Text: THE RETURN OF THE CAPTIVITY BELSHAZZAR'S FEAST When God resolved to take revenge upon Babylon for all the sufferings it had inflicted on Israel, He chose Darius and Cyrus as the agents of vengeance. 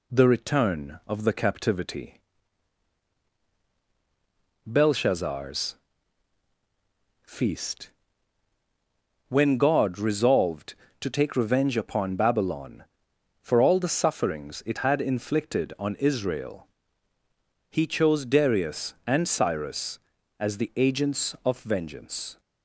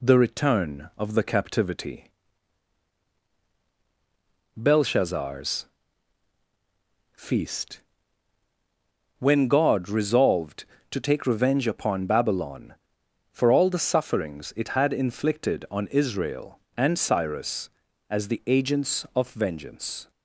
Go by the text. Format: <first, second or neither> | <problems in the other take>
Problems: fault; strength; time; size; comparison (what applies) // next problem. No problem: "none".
first | pauses between "CAPTIVITY" and "BELSHAZZAR'S"; strong; at 2.0 s; 2.4 s long; strong in the first // pauses between "BELSHAZZAR'S" and "FEAST"; strong; at 5.6 s; 1.4 s long; strong in the first // pauses between "FEAST" and "When"; strong; at 7.8 s; 1.3 s long; strong in the first // skips "He chose Darius"; at 16.6 s